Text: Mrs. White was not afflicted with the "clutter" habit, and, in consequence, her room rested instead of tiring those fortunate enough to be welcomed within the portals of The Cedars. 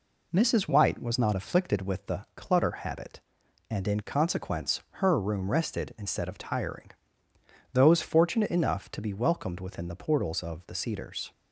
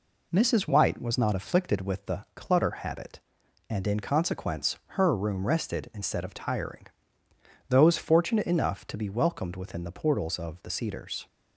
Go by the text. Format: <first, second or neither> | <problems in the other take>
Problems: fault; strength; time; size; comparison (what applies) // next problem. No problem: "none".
neither | pauses between "tiring" and "those"; noticeable; the same in both